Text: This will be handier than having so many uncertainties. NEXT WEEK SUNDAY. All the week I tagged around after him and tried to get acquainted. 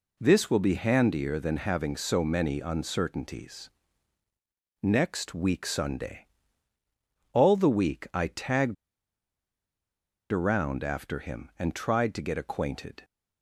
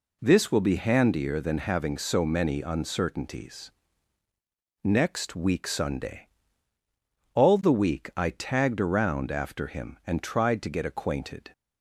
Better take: second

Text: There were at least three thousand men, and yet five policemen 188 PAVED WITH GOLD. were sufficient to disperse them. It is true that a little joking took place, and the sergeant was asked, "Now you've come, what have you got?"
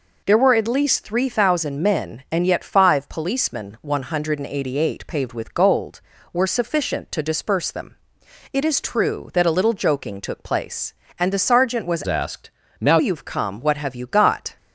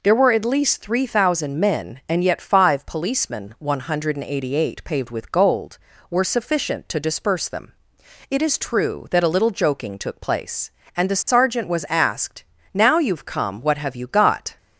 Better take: second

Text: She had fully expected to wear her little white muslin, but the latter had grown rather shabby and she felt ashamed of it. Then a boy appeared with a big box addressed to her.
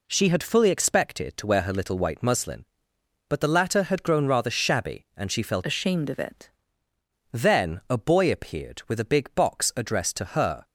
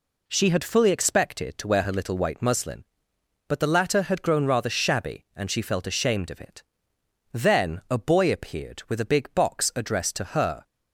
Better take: second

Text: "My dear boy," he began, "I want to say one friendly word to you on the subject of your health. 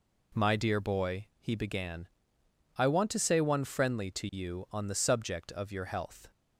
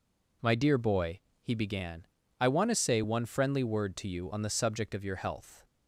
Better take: second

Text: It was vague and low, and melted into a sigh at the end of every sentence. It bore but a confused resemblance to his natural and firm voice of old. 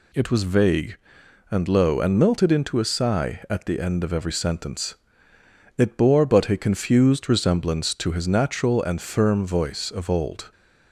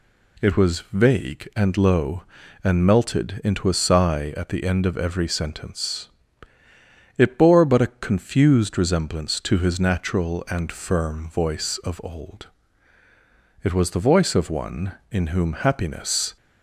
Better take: first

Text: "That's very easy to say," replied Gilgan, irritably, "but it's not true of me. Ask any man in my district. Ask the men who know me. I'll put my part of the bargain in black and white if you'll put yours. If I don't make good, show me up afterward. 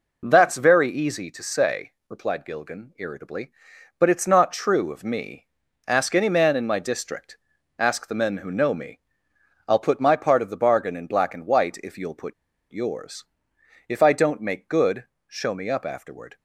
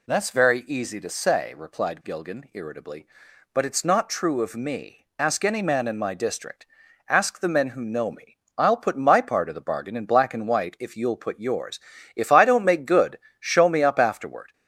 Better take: second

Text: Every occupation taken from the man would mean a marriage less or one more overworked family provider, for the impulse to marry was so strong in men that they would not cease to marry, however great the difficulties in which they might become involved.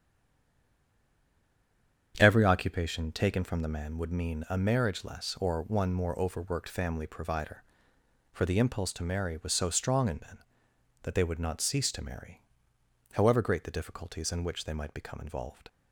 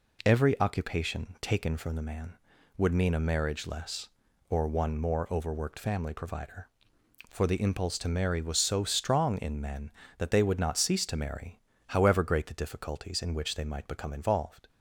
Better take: second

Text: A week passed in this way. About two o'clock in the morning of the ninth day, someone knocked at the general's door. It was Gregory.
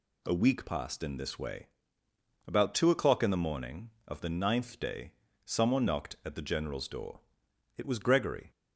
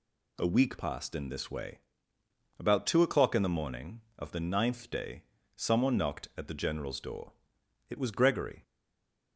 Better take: first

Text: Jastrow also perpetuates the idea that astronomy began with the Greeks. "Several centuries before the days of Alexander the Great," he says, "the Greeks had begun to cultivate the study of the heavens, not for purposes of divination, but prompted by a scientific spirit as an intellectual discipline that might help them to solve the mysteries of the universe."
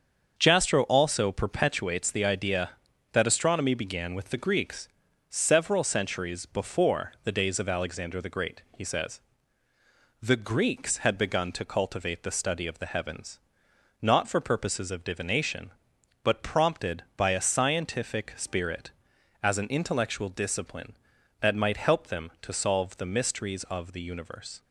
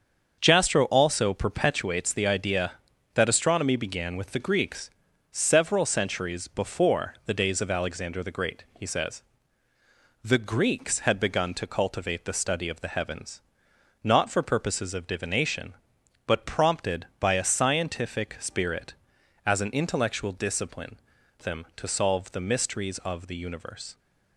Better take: first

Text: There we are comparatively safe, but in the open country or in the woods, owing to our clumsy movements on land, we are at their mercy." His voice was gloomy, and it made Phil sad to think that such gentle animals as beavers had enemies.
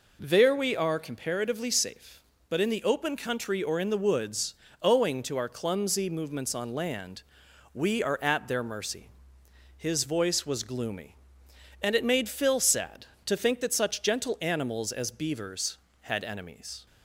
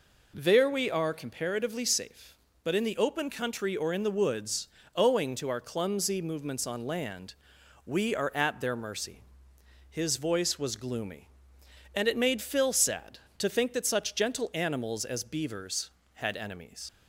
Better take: first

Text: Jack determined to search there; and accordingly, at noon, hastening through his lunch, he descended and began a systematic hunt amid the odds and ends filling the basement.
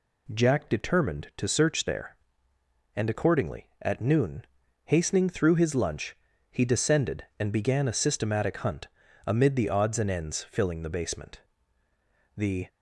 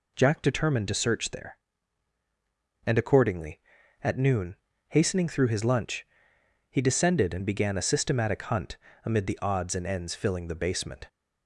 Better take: second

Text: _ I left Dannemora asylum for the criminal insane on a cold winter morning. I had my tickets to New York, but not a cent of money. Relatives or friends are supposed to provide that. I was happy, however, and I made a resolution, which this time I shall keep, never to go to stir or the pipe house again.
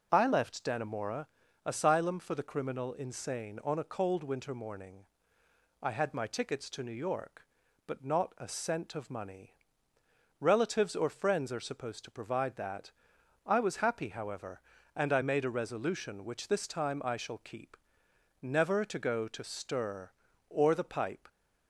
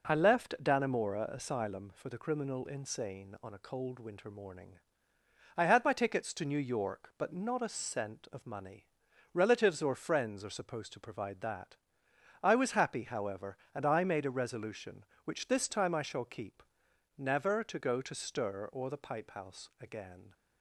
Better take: second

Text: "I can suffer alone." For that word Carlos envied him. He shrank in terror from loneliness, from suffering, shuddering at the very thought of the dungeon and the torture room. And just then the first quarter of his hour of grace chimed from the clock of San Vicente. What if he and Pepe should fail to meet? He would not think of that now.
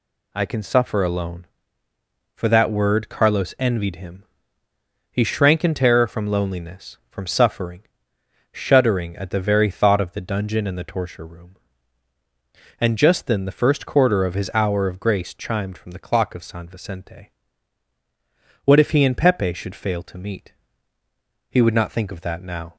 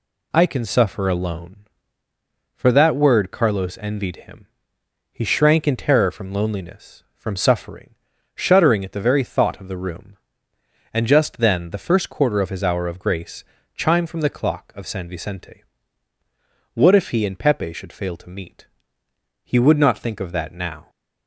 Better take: first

